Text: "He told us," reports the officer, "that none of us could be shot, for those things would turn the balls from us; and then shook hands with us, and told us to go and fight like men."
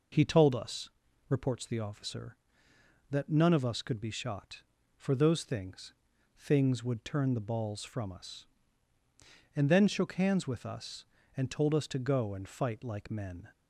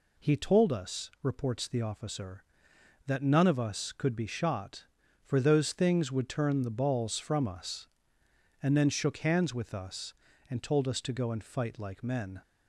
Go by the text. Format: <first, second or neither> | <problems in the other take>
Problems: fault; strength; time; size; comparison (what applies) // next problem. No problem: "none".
second | says "things" twice; at 6.3 s